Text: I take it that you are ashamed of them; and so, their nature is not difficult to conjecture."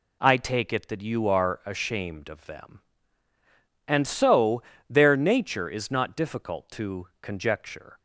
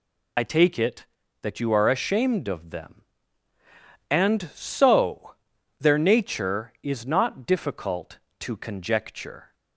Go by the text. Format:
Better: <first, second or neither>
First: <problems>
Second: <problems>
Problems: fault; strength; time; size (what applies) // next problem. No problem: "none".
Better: first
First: none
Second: loses the start of "I"; at 0.3 s; 50 ms